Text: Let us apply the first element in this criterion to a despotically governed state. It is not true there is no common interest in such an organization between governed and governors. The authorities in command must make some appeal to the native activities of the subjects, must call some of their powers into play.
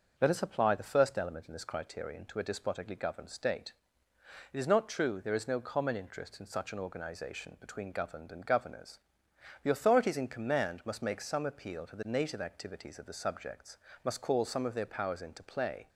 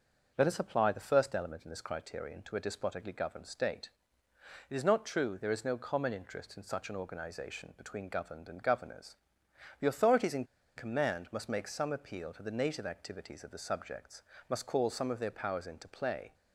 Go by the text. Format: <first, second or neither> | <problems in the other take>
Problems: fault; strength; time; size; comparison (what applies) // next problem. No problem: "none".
first | starts louder than the rest; noticeable; until 1.3 s; 6 dB; noticeable in the first // pauses between "in" and "command"; slight; at 10.4 s; 0.32 s long